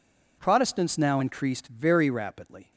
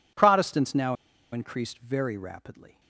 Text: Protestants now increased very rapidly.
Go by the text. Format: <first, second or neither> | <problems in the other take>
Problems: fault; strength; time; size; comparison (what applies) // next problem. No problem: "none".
first | pauses between "now" and "increased"; at 0.9 s; 0.37 s long